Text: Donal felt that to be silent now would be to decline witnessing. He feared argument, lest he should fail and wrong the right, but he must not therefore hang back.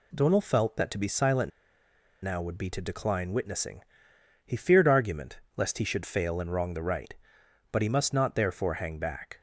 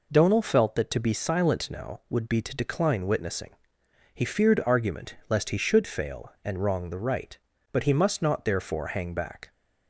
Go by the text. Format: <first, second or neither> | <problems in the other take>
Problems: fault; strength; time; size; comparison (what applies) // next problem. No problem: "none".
second | pauses between "silent" and "now"; noticeable; at 1.5 s; 0.74 s long